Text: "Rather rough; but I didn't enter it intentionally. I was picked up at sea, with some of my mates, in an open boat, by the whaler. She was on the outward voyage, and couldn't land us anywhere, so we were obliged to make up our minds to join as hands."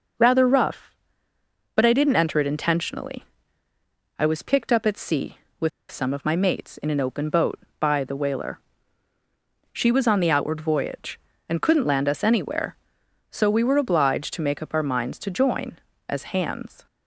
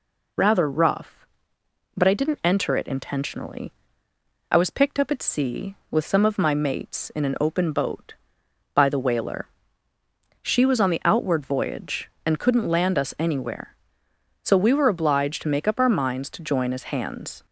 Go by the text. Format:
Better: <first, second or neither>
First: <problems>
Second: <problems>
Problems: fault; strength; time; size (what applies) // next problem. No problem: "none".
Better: second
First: pauses between "with" and "some"; slight; at 5.6 s; 0.21 s long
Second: none